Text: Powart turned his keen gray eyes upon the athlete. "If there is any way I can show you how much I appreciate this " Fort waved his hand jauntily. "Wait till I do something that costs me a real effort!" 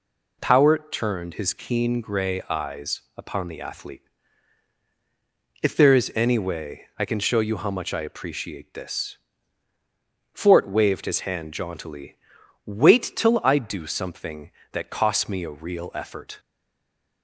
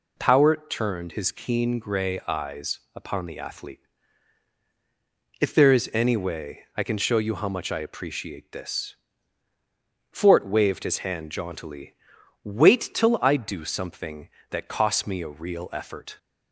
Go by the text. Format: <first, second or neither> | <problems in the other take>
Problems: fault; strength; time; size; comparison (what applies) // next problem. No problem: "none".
second | pauses between "eyes" and "upon"; slight; at 3.0 s; 0.16 s long; slight in the second // stays silent after the last word; slight; from 16.3 s on; 0.9 s long